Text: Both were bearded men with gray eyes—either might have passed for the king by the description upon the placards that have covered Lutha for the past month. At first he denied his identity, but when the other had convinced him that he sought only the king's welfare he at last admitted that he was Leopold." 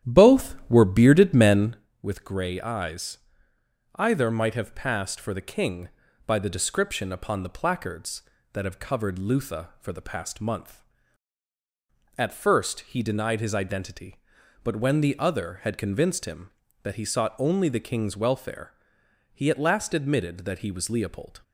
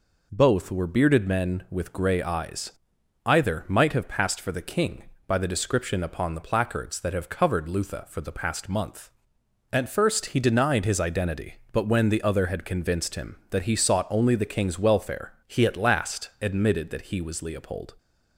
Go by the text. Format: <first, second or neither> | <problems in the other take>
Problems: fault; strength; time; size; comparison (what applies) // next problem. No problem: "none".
second | starts louder than the rest; strong; until 1.8 s; 10.5 dB // pauses between "welfare" and "he"; noticeable; at 18.7 s; 0.60 s long